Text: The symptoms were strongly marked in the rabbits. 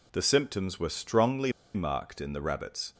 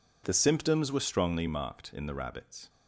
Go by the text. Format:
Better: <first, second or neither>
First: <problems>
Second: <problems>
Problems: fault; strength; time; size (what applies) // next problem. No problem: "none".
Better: second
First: pauses between "strongly" and "marked"; slight; at 1.5 s; 0.23 s long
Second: none